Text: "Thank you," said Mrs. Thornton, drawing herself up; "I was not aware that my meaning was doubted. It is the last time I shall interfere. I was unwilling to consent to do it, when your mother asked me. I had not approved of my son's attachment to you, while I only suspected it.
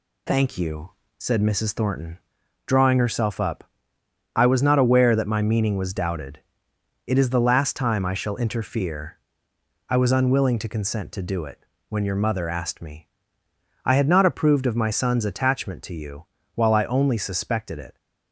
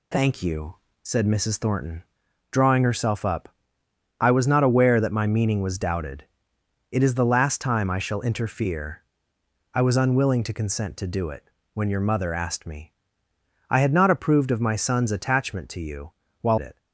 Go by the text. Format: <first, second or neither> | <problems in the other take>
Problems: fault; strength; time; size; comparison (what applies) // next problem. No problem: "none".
first | skips "I only suspected"; at 16.5 s